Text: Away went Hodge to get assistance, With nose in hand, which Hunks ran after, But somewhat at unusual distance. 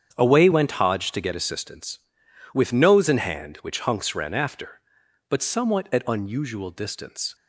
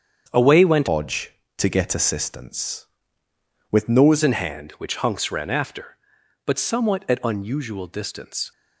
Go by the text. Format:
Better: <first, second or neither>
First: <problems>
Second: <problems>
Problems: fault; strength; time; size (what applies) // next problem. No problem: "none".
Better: first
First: starts louder than the rest; strong; until 1.2 s; 8 dB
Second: starts louder than the rest; strong; until 1.3 s; 7.5 dB // changes voice from "Hodge" to "nose"; from 0.8 to 4.2 s; 3.4 s long